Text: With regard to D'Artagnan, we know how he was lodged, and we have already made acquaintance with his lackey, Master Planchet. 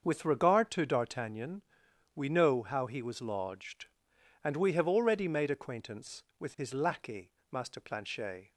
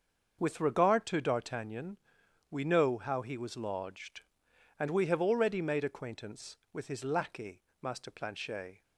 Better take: neither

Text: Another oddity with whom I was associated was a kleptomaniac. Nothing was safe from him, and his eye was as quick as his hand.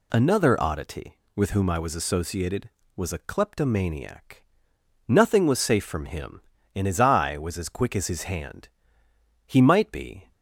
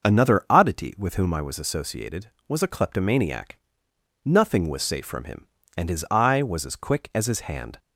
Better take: second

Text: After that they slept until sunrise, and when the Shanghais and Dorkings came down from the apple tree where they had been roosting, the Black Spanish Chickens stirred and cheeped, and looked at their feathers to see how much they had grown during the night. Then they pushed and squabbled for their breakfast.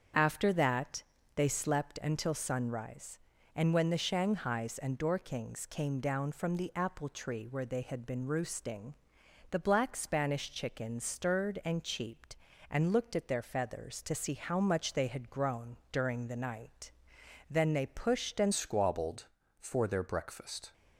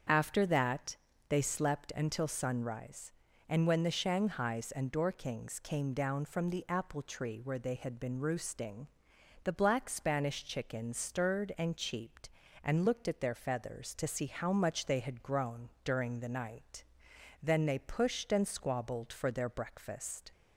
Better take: second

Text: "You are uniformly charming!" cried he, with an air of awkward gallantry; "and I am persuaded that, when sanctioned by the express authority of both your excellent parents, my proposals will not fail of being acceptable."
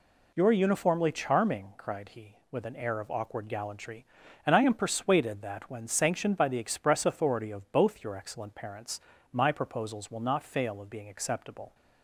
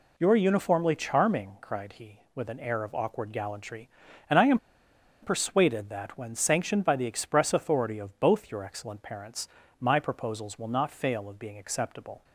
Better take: first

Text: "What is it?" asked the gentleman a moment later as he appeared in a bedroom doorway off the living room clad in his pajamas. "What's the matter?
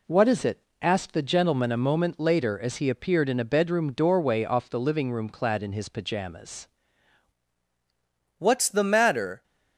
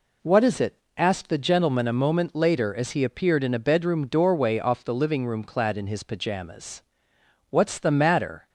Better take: second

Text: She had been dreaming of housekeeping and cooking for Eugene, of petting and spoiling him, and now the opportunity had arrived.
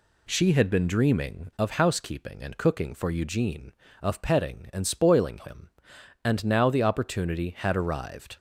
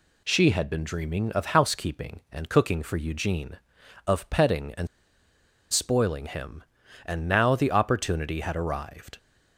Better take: first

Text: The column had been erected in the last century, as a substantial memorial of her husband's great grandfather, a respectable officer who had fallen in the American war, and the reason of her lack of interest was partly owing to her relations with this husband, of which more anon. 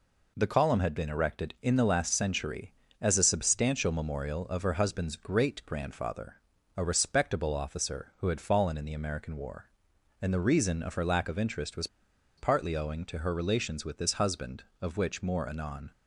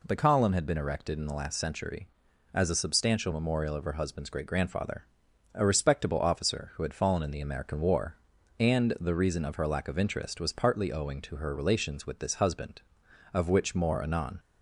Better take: second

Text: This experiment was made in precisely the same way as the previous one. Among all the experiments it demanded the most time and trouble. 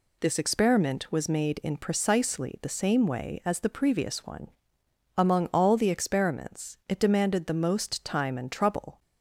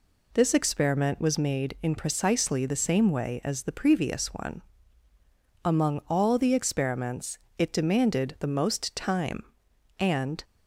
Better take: first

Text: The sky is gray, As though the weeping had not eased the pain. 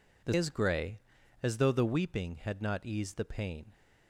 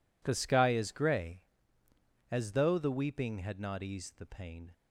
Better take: second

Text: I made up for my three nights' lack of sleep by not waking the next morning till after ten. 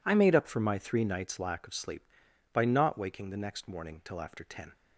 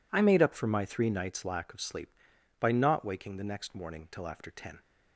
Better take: neither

